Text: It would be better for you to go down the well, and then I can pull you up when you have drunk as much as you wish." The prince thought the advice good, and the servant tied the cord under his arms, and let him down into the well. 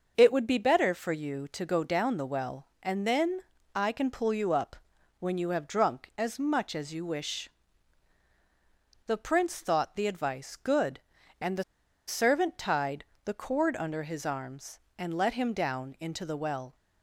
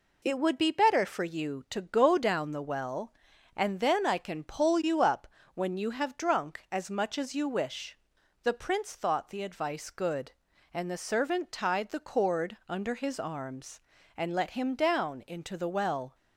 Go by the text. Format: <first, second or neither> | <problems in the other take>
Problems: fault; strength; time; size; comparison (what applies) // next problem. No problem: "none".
second | starts louder than the rest; noticeable; until 1.1 s; 6 dB // pauses between "then" and "I"; slight; at 3.4 s; 0.34 s long // pauses between "up" and "when"; at 4.7 s; 0.42 s long; slight in the second // pauses between "the" and "servant"; at 11.6 s; 0.45 s long // pauses between "tied" and "the"; slight; at 13.0 s; 0.18 s long